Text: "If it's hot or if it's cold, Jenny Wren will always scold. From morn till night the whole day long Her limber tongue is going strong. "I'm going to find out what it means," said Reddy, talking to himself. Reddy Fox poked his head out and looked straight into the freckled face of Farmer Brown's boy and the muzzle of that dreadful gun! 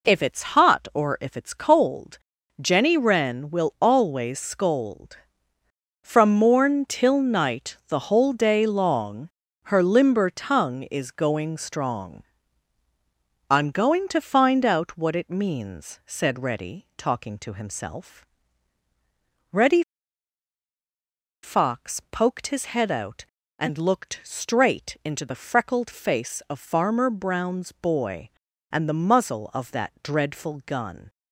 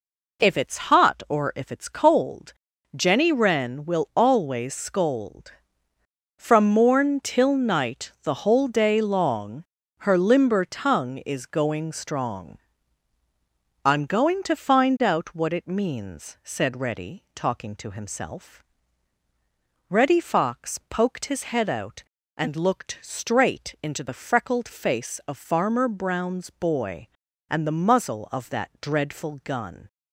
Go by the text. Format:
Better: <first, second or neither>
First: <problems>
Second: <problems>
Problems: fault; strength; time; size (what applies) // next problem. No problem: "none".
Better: second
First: pauses between "long" and "Her"; slight; at 9.2 s; 0.34 s long // pauses between "Reddy" and "Fox"; strong; at 19.8 s; 1.6 s long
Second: pauses between "long" and "Her"; slight; at 9.6 s; 0.34 s long